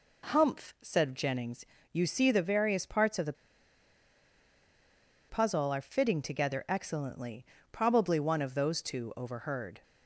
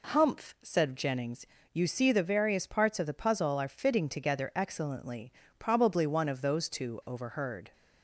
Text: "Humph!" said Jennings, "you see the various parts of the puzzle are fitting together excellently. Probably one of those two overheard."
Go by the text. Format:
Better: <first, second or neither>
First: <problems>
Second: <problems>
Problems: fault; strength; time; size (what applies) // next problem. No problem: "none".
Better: second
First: pauses between "the" and "puzzle"; strong; at 3.3 s; 1.9 s long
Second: none